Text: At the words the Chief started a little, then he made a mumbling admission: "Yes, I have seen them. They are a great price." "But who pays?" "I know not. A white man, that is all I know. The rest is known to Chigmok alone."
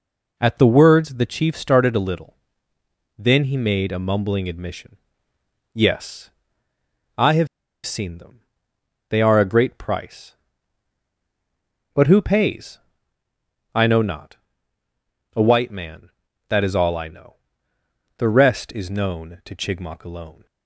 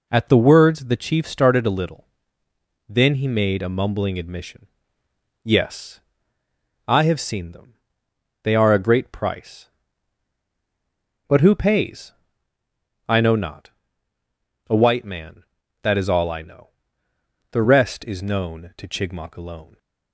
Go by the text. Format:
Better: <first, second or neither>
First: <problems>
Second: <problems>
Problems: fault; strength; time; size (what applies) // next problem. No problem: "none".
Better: second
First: pauses between "have" and "seen"; at 7.4 s; 0.38 s long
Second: none